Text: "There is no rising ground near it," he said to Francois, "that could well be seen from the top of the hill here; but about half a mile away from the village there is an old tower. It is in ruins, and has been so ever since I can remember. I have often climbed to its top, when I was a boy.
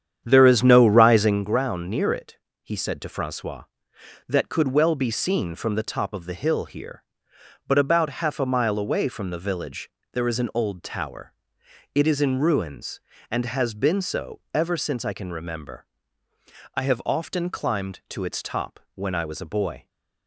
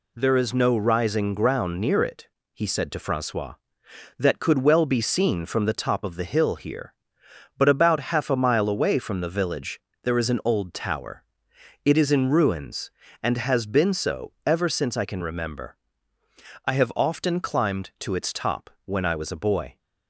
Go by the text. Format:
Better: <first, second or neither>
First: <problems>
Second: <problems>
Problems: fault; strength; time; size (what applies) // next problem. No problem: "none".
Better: second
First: starts louder than the rest; strong; until 1.5 s; 9 dB // pauses between "village" and "there"; slight; at 9.8 s; 0.24 s long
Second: pauses between "village" and "there"; slight; at 9.7 s; 0.24 s long